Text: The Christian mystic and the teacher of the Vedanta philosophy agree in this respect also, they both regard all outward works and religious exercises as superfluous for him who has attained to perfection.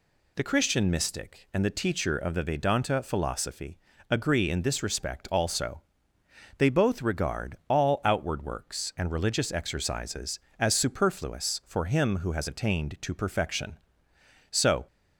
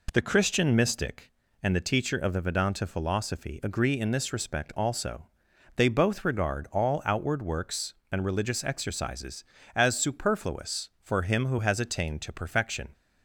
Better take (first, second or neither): second